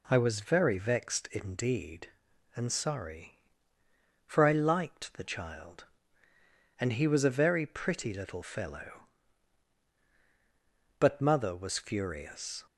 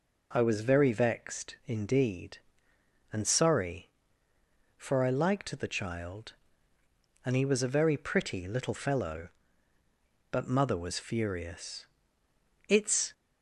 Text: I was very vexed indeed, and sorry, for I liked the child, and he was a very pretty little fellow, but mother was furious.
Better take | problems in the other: first | goes on to say "It's"; slight; from 12.6 s on; 0.42 s long

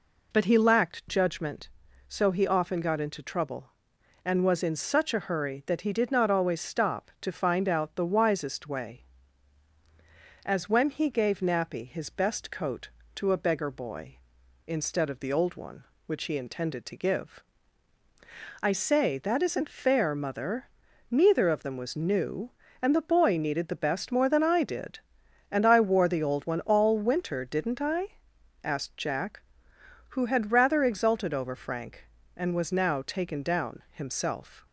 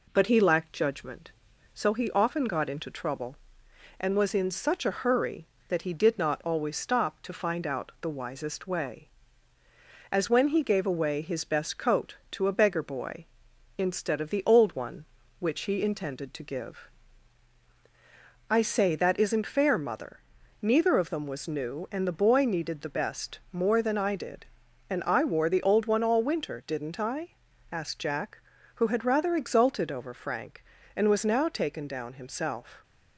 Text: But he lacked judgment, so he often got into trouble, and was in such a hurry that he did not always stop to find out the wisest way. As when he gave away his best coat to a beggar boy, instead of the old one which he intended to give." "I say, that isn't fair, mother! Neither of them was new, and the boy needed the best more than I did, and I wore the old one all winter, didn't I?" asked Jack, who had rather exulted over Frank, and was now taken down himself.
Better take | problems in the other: second | says "nappy" for "away"; at 11.3 s

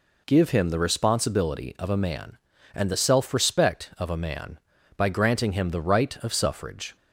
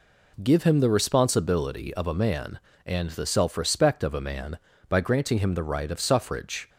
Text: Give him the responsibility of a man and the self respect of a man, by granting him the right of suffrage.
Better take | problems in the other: neither | none

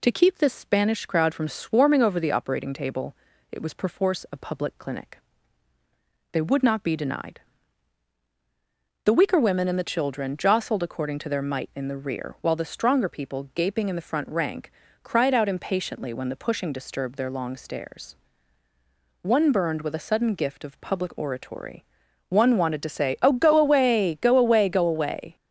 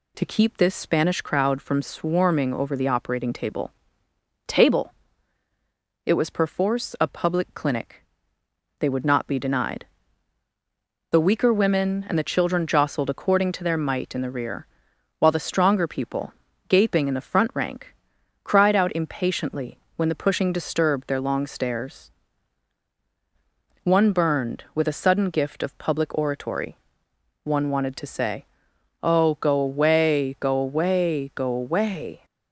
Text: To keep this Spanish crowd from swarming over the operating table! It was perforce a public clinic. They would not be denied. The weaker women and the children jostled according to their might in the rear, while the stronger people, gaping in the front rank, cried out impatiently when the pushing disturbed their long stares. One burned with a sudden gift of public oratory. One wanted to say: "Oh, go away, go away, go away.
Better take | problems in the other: first | says "table" twice; at 4.4 s // pauses between "impatiently" and "when"; slight; at 19.7 s; 0.18 s long

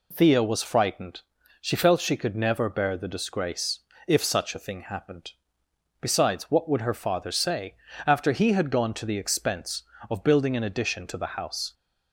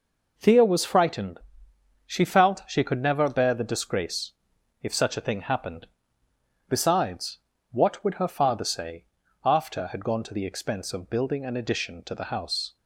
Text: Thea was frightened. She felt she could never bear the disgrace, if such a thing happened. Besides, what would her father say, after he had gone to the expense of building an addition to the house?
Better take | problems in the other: first | skips "he"; at 9.8 s

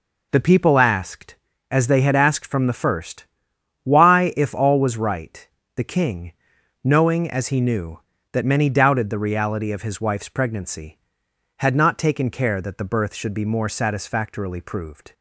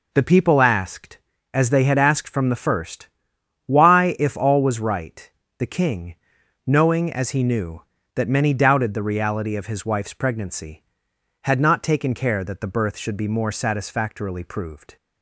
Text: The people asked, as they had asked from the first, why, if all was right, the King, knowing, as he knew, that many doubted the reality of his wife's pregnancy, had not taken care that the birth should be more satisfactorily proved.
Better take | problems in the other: neither | none

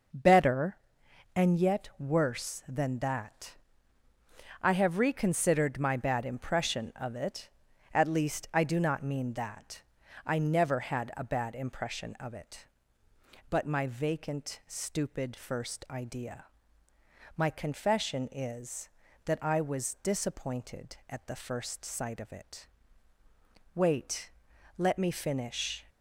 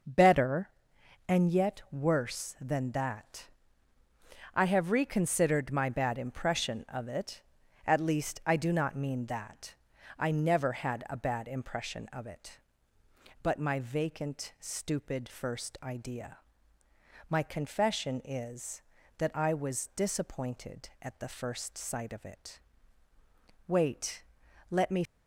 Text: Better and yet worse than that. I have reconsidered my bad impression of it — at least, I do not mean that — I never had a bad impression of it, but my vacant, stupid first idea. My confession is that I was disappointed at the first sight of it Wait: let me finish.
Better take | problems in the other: first | pauses between "it" and "Wait"; at 22.5 s; 1.0 s long; also in the first // stops before "finish"; at 25.0 s

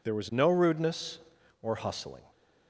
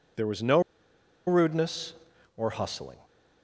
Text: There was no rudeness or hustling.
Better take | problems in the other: first | pauses between "no" and "rudeness"; noticeable; at 0.5 s; 0.66 s long

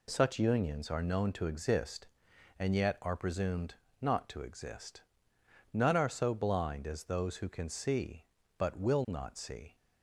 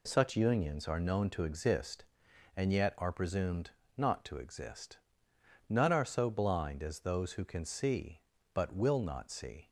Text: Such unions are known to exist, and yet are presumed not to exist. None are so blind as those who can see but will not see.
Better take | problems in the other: neither | pauses between "presumed" and "not"; slight; the same in both

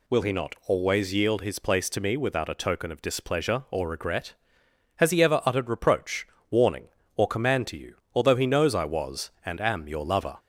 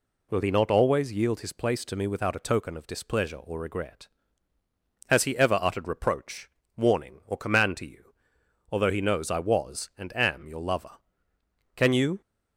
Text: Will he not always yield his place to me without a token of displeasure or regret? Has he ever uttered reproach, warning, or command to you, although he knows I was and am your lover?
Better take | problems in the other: first | goes on to say "Can you"; slight; from 11.7 s on; 0.46 s long

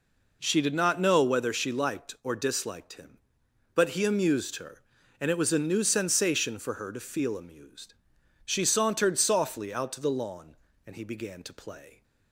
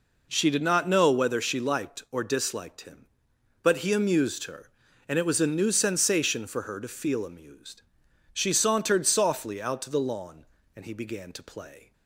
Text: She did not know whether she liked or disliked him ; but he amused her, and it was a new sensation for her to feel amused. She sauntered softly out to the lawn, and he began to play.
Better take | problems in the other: neither | none

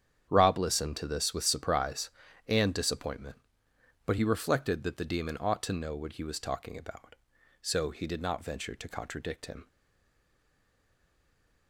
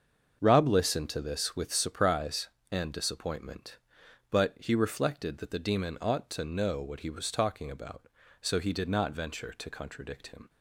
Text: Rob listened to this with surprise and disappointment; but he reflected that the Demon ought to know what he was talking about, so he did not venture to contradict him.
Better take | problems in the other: second | starts louder than the rest; strong; until 1.3 s; 9 dB; also in the second // stays silent after the last word; noticeable; from 9.6 s on; 2.0 s long

